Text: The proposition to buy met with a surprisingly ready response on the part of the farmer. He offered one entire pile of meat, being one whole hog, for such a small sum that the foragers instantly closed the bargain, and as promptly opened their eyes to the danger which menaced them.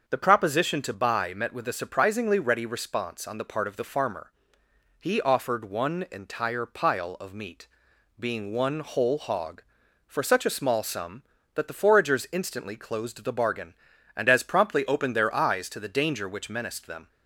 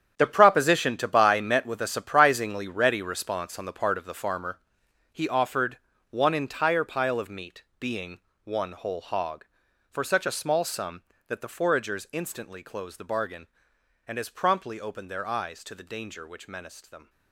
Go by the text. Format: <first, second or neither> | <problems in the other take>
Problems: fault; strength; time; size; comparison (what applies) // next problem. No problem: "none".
first | gets quieter; strong; throughout; 13 dB // starts louder than the rest; strong; until 1.2 s; 9 dB; also in the first // pauses between "offered" and "one"; slight; at 5.7 s; 0.32 s long // pauses between "being" and "one"; slight; at 8.1 s; 0.24 s long